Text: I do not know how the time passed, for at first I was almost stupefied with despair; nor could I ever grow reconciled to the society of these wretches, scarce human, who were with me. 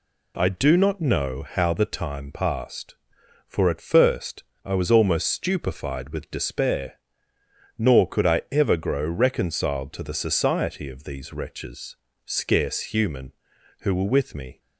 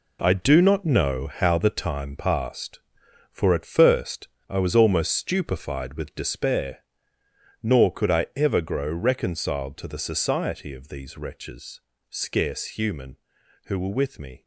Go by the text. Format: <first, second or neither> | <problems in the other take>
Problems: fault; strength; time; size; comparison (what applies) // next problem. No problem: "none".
first | gets quieter; strong; throughout; 8.5 dB // pauses between "first" and "I"; slight; at 4.2 s; 0.22 s long; slight in the first